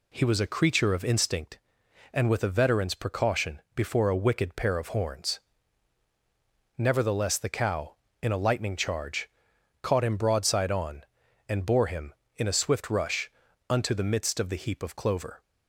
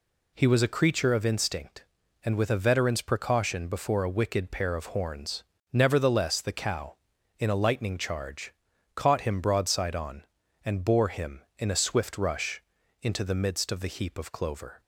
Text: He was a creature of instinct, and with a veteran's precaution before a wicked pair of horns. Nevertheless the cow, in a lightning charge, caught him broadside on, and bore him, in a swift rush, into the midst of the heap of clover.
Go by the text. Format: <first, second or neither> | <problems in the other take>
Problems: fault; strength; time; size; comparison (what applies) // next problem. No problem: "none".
second | says "unto" for "into"; at 13.7 s